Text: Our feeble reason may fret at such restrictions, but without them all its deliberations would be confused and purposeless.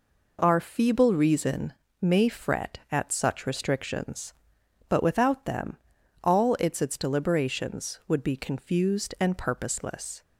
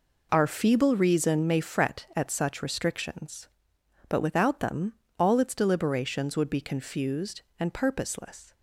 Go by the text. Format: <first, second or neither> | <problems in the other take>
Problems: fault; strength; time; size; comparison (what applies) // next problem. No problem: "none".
second | pauses between "reason" and "may"; slight; at 1.7 s; 0.26 s long // pauses between "them" and "all"; noticeable; at 5.7 s; 0.48 s long; slight in the second // says "its" twice; at 6.7 s